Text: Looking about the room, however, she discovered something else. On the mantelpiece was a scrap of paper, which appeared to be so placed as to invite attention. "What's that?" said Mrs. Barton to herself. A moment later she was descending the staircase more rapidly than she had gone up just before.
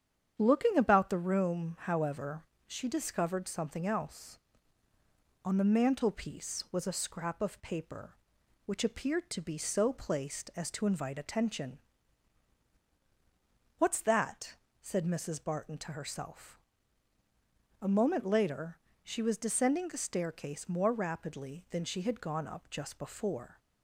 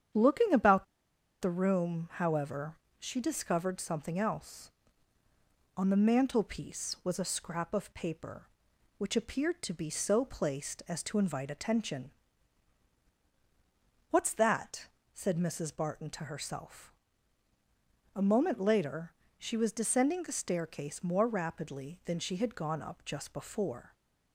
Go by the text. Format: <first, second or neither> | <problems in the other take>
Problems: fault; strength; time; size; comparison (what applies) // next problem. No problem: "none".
first | starts louder than the rest; strong; until 1.7 s; 8.5 dB; strong in the first // pauses between "about" and "the"; noticeable; at 0.8 s; 0.58 s long // pauses between "later" and "she"; slight; at 19.1 s; 0.26 s long; slight in the first